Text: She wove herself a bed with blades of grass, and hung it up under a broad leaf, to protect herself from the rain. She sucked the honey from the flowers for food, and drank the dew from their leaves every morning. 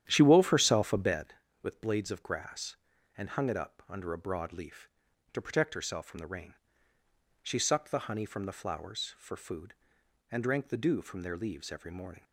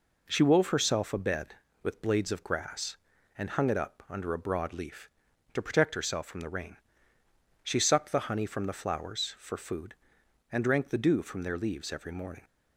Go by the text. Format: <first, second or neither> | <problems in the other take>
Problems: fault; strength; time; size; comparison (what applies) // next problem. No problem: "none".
second | starts louder than the rest; strong; until 1.2 s; 10.5 dB